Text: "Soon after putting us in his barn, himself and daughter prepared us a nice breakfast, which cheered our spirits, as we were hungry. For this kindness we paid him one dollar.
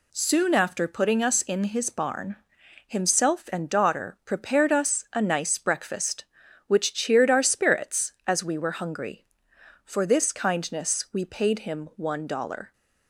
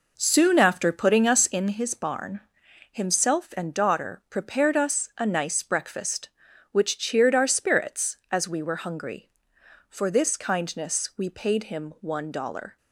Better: first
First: none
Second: starts louder than the rest; noticeable; until 1.8 s; 4.5 dB

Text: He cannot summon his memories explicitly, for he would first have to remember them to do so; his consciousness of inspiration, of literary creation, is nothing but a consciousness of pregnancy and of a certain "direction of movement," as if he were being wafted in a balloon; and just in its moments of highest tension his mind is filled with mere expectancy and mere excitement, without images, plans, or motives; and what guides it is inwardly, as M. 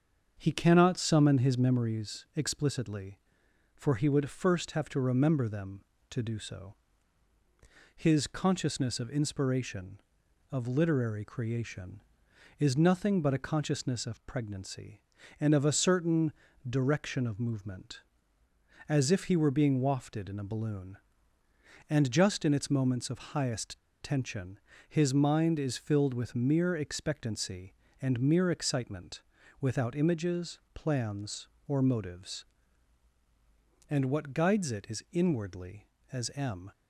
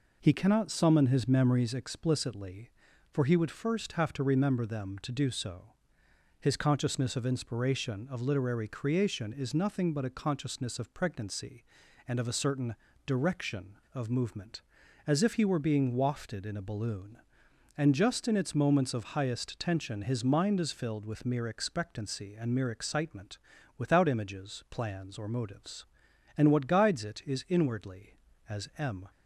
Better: second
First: starts louder than the rest; until 1.3 s; 7 dB // pauses between "certain" and "direction"; slight; at 16.3 s; 0.36 s long // pauses between "highest" and "tension"; slight; at 23.7 s; 0.24 s long // pauses between "tension" and "his"; slight; at 24.5 s; 0.32 s long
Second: pauses between "certain" and "direction"; slight; at 12.7 s; 0.32 s long

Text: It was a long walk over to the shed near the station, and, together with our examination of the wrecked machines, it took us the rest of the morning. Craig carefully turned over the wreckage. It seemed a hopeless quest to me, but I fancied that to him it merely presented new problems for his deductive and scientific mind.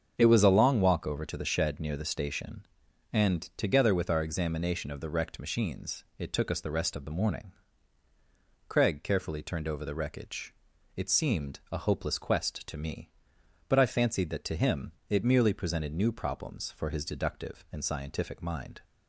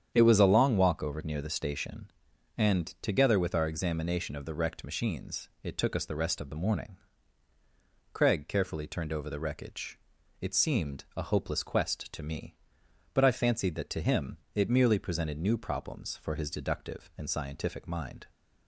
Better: first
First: starts louder than the rest; until 1.1 s; 7 dB // pauses between "him" and "it"; slight; at 14.9 s; 0.16 s long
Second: starts louder than the rest; strong; until 1.1 s; 8.5 dB // skips "to the shed"; at 1.2 s // pauses between "him" and "it"; slight; at 14.3 s; 0.16 s long

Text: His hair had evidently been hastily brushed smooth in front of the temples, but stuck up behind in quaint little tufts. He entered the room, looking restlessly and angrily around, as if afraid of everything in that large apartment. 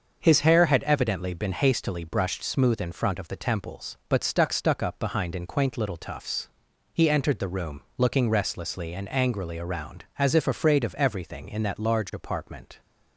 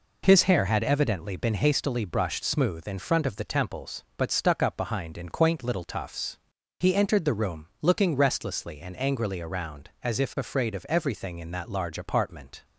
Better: second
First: starts louder than the rest; until 1.2 s; 6.5 dB // says "stuck" twice; at 4.5 s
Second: none

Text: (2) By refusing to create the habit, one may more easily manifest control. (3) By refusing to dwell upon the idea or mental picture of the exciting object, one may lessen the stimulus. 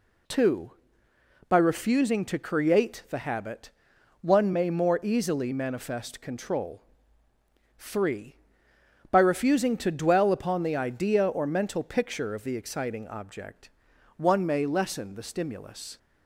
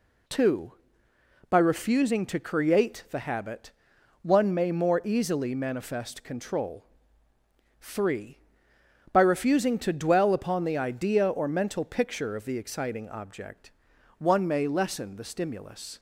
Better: neither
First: none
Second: none

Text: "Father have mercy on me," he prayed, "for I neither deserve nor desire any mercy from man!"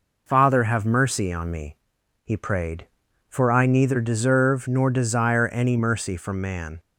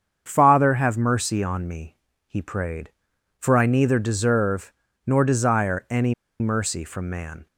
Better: first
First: none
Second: starts louder than the rest; strong; until 1.2 s; 7.5 dB // pauses between "deserve" and "nor"; slight; at 4.7 s; 0.34 s long // pauses between "any" and "mercy"; slight; at 6.1 s; 0.26 s long

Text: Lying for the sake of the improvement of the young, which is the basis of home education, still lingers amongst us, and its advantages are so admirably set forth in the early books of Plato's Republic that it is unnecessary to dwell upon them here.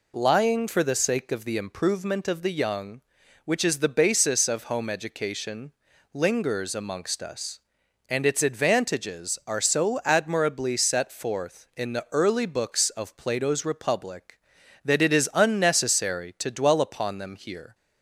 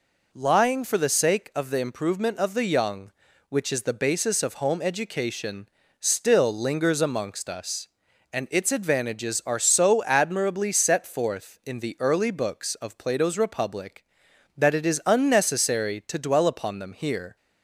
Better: second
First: skips "still"; at 5.9 s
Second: none

